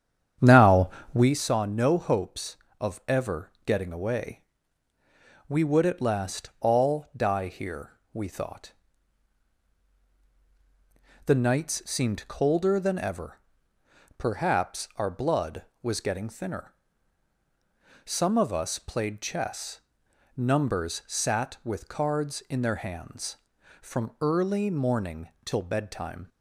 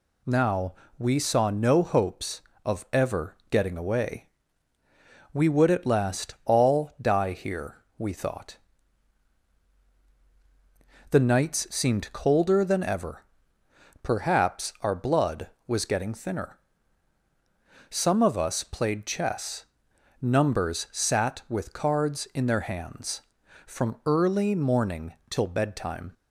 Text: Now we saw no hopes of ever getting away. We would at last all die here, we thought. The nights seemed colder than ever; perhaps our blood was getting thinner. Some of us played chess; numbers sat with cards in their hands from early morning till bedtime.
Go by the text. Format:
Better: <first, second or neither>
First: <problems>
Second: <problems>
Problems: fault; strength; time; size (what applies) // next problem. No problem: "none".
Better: second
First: starts louder than the rest; strong; until 1.3 s; 8.5 dB // pauses between "Now" and "we"; slight; at 0.8 s; 0.24 s long // pauses between "morning" and "till"; slight; at 25.2 s; 0.16 s long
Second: pauses between "Now" and "we"; slight; at 0.7 s; 0.24 s long // pauses between "morning" and "till"; slight; at 25.1 s; 0.16 s long